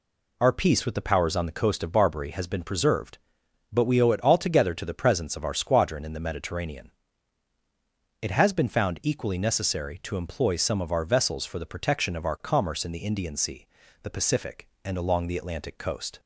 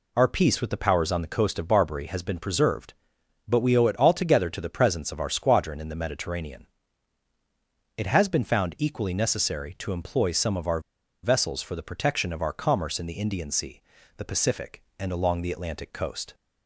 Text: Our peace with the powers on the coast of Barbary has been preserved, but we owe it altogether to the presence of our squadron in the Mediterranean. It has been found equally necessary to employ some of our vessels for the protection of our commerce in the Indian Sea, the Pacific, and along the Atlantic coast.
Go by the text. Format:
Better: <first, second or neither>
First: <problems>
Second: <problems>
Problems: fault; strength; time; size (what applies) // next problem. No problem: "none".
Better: first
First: none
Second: pauses between "our" and "vessels"; at 10.7 s; 0.43 s long